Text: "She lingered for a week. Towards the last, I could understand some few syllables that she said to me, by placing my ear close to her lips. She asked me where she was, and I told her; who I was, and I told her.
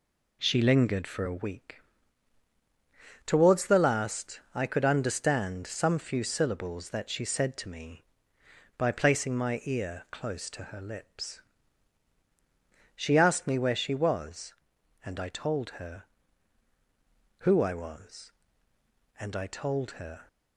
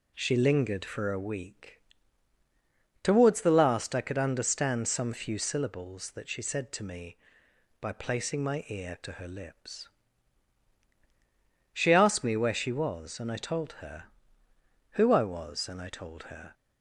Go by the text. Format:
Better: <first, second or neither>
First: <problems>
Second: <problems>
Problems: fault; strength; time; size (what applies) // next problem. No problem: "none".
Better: first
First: none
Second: skips "close"; at 8.9 s